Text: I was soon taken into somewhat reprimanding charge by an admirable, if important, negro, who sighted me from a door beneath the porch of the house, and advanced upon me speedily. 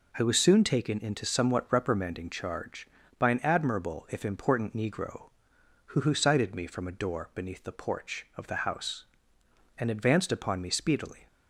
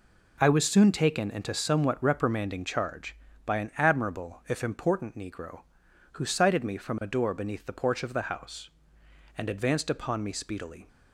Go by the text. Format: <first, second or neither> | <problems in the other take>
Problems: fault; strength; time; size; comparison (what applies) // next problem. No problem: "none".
second | says "who" twice; at 6.0 s